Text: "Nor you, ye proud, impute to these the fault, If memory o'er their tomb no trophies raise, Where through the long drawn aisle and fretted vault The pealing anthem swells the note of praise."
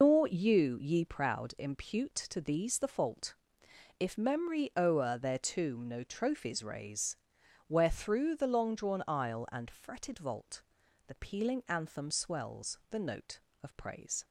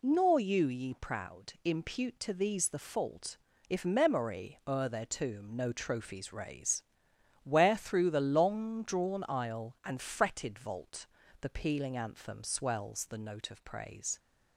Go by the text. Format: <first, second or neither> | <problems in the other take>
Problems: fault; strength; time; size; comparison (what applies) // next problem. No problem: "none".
second | loses the start of "Nor"; at 0.0 s; 125 ms // pauses between "vault" and "The"; at 10.6 s; 0.44 s long; slight in the second